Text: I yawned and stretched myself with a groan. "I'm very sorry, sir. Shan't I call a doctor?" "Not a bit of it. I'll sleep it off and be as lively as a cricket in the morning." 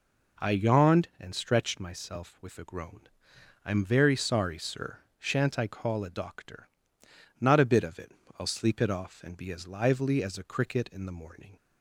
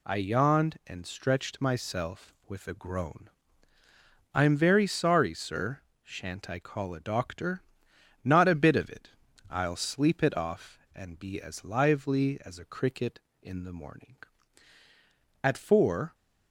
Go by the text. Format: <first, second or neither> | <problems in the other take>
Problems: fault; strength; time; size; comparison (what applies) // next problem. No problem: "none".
first | goes on to say "At four"; noticeable; from 15.4 s on; 0.72 s long